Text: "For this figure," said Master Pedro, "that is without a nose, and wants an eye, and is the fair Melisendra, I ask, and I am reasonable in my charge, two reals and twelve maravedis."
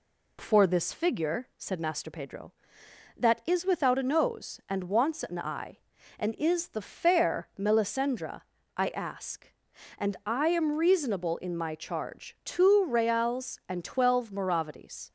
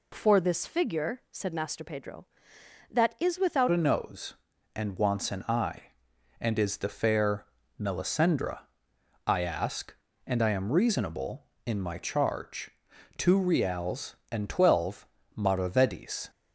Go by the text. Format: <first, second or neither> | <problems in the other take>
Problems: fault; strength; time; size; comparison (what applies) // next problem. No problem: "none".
first | changes voice at "a"; from 3.6 s on; 12.6 s long // pauses between "fair" and "Melisendra"; slight; at 7.4 s; 0.32 s long // pauses between "twelve" and "maravedis"; slight; at 15.0 s; 0.30 s long